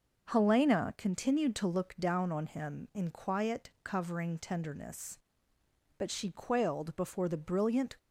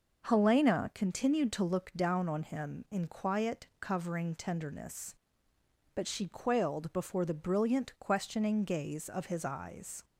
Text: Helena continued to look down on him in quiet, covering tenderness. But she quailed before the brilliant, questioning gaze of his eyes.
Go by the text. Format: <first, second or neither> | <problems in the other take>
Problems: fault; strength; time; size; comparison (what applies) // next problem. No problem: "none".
second | starts louder than the rest; until 1.3 s; 6 dB; noticeable in the second // stops before "questioning gaze of his eyes"; at 7.9 s